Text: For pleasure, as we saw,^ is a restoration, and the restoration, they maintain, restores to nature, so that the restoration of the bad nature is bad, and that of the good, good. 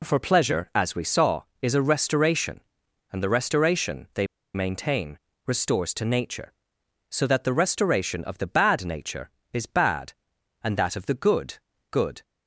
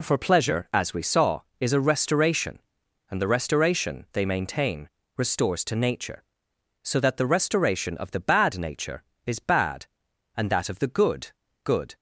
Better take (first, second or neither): second